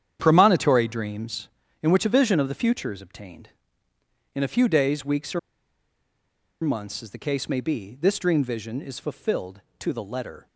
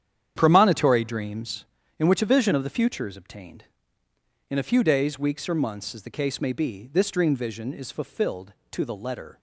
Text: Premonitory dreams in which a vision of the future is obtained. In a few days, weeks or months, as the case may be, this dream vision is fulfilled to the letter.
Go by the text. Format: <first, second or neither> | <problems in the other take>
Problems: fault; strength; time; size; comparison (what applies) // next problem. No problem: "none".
second | starts louder than the rest; strong; until 1.2 s; 9 dB; strong in the second // pauses between "or" and "months"; at 5.3 s; 1.2 s long